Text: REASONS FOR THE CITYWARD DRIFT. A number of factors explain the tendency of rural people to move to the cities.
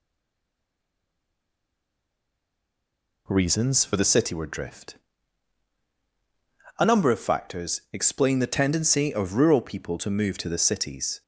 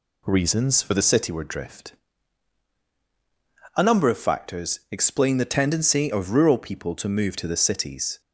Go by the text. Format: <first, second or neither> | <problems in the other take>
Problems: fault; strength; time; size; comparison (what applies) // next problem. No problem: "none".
second | stays silent before the first word; strong; until 3.2 s; 3.2 s long